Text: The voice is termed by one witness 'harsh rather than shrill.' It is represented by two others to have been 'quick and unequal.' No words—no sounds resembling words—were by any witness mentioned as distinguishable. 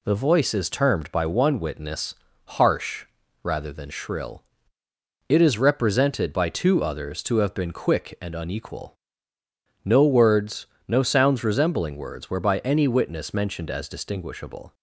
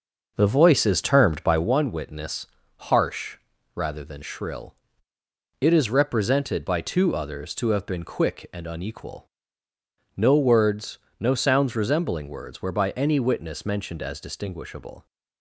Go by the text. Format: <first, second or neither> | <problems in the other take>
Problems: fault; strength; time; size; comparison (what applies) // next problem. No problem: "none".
first | starts louder than the rest; noticeable; until 1.7 s; 6 dB // pauses between "witness" and "harsh"; slight; at 2.4 s; 0.28 s long; slight in the first // pauses between "harsh" and "rather"; at 3.3 s; 0.38 s long; also in the first